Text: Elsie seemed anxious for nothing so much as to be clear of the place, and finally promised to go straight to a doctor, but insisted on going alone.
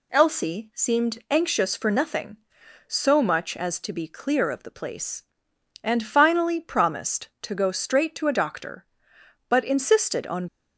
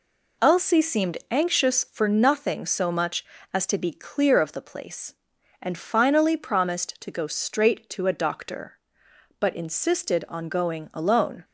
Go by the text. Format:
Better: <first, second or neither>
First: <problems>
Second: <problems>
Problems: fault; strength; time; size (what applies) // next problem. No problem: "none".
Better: second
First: stops before "going alone"; at 10.4 s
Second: none